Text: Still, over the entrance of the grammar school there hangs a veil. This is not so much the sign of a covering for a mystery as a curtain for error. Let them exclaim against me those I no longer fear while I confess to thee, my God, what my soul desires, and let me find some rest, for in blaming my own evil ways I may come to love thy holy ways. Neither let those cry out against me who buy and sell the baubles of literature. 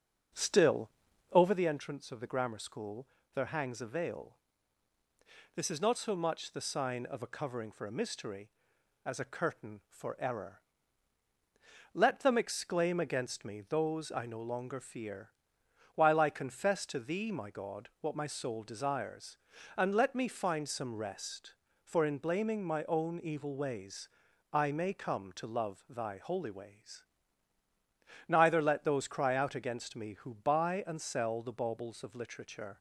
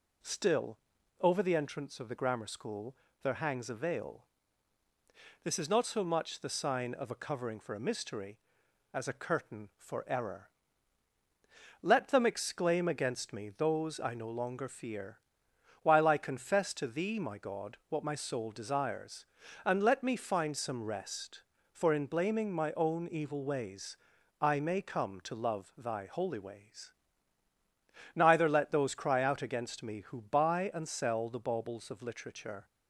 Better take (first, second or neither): second